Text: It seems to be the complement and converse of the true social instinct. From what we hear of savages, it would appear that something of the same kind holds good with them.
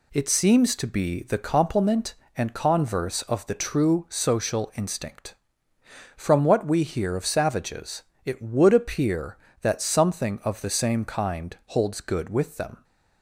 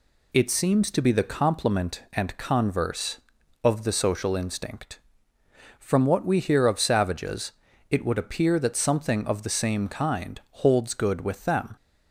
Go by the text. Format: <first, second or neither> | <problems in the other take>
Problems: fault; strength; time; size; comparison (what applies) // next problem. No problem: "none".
first | skips "true"; at 3.9 s